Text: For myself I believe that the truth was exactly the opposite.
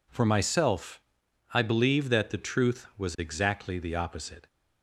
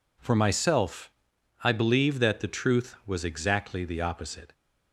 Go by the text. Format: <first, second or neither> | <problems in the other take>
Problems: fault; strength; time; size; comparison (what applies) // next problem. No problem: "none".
neither | pauses between "myself" and "I"; noticeable; the same in both